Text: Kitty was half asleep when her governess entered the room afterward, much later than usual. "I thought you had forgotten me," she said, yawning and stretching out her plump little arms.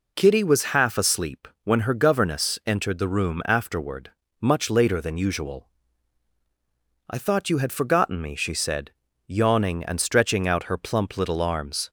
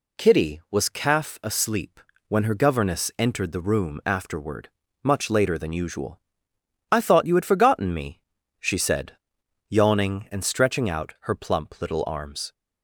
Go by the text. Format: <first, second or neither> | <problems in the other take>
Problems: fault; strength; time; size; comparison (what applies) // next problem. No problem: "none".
first | says "calf" for "half"; at 0.8 s // pauses between "asleep" and "when"; slight; at 1.9 s; 0.28 s long; slight in the first